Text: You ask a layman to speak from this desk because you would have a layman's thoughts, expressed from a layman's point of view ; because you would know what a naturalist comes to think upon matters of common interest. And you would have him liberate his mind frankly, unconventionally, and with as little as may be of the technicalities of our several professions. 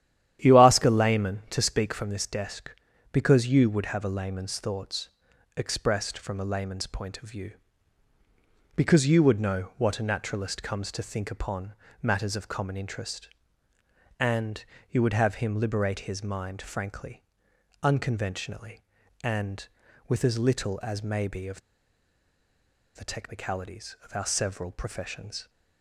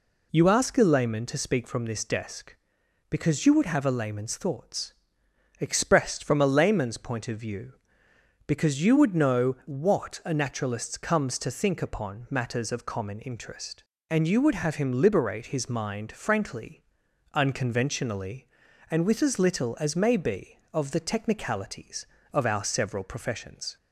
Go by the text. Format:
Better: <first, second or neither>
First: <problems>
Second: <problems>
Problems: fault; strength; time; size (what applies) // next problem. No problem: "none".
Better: second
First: starts louder than the rest; strong; until 1.4 s; 11 dB // pauses between "upon" and "matters"; slight; at 11.7 s; 0.26 s long // pauses between "And" and "you"; slight; at 14.6 s; 0.26 s long // pauses between "of" and "the"; strong; at 21.5 s; 1.3 s long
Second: none